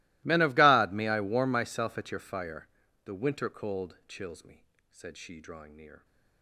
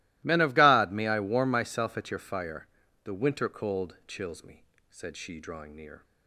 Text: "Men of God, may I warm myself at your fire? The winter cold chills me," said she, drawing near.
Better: second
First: gets quieter; strong; throughout; 26.5 dB // starts louder than the rest; strong; until 1.2 s; 20.5 dB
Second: starts louder than the rest; strong; until 1.2 s; 17.5 dB

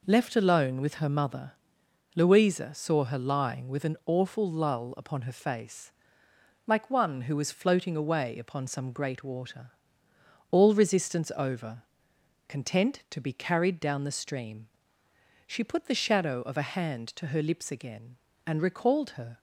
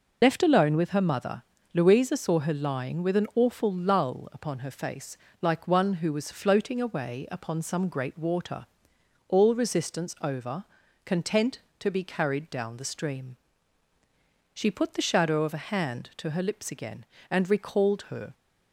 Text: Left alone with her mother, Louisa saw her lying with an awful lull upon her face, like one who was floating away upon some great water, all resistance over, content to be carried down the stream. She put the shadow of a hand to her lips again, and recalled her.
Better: first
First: none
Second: loses the start of "Left"; at 0.2 s; 30 ms

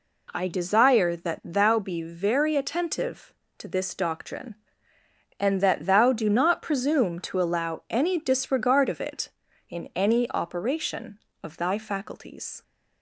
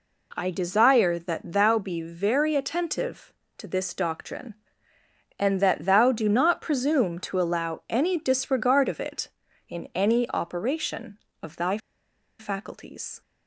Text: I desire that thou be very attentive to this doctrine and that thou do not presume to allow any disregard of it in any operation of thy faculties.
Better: first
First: none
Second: pauses between "thy" and "faculties"; noticeable; at 11.7 s; 0.61 s long

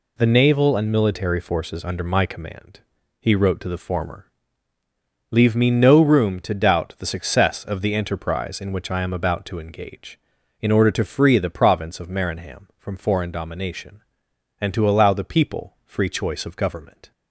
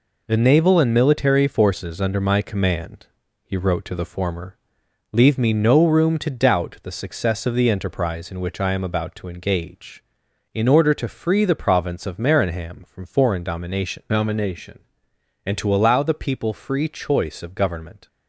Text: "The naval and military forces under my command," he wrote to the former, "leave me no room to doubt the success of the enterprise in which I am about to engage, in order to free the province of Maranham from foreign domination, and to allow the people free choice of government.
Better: first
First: none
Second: says "domination" twice; at 14.0 s

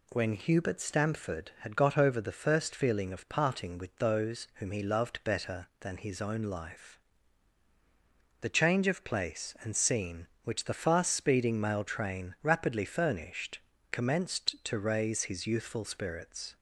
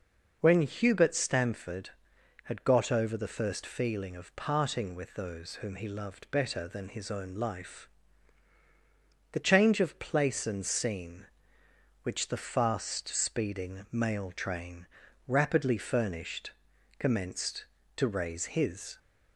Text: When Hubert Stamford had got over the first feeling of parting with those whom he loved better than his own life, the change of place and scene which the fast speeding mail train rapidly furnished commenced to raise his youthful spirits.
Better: first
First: pauses between "furnished" and "commenced"; slight; at 13.5 s; 0.32 s long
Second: pauses between "train" and "rapidly"; at 14.8 s; 0.40 s long // pauses between "furnished" and "commenced"; noticeable; at 16.5 s; 0.46 s long // stops before "youthful spirits"; at 18.9 s

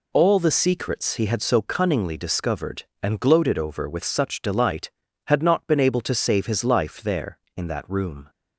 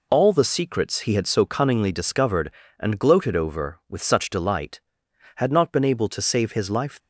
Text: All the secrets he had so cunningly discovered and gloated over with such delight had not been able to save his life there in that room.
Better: first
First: none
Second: stops before "there in that room"; at 6.9 s

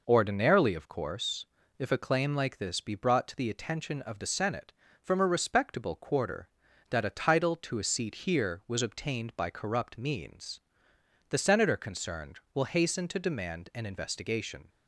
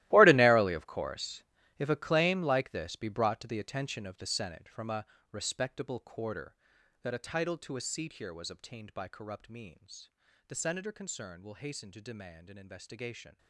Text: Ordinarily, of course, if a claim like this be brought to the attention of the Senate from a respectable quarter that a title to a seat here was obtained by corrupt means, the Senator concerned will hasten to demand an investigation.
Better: first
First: none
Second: gets quieter; strong; throughout; 16.5 dB // pauses between "a" and "respectable"; slight; at 5.0 s; 0.26 s long

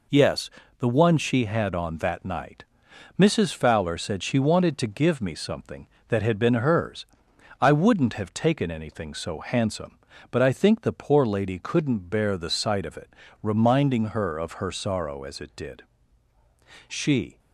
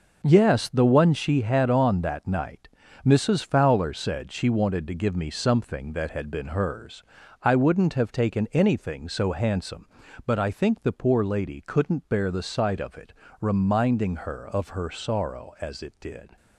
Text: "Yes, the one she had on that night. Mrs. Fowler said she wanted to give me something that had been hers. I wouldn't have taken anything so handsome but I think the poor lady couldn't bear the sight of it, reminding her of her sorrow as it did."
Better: second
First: goes on to say "She"; from 16.8 s on; 0.50 s long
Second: none

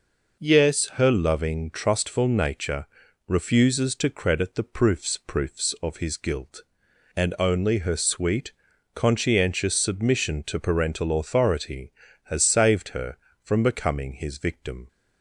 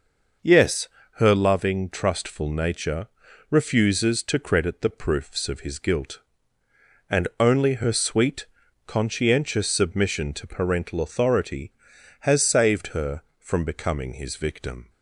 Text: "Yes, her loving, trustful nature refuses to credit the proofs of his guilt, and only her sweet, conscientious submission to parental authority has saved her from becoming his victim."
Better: second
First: pauses between "nature" and "refuses"; at 2.8 s; 0.42 s long // says "proofs" twice; at 5.1 s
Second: pauses between "nature" and "refuses"; at 3.0 s; 0.42 s long

